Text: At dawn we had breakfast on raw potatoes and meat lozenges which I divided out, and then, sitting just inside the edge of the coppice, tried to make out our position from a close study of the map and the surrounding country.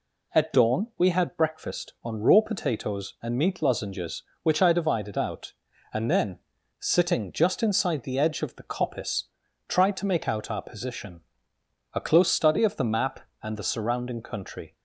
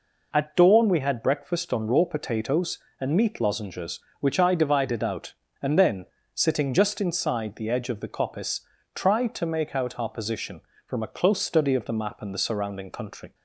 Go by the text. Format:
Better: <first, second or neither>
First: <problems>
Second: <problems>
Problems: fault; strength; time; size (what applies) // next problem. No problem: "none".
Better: second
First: skips "from"; at 11.5 s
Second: none